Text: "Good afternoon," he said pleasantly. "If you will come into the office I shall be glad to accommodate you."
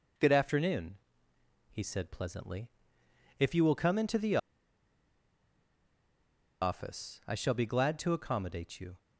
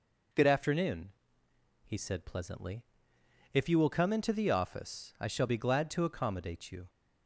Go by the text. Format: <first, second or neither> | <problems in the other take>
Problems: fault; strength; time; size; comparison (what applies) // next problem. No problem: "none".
second | pauses between "the" and "office"; strong; at 4.3 s; 2.2 s long